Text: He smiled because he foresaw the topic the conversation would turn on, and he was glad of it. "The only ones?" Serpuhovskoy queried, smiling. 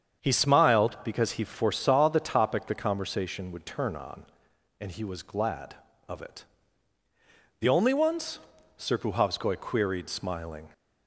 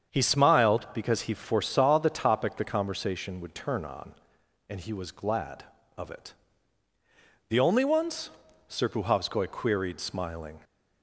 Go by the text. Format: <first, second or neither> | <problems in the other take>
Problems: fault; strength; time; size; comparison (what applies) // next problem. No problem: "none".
neither | starts louder than the rest; strong; the same in both